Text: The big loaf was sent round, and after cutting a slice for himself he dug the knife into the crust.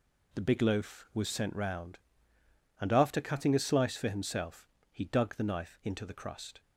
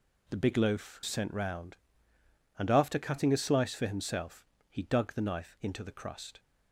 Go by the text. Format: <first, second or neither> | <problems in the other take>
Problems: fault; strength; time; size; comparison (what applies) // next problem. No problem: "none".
first | skips "was"; at 1.0 s // pauses between "himself" and "he"; slight; at 4.4 s; 0.20 s long; slight in the first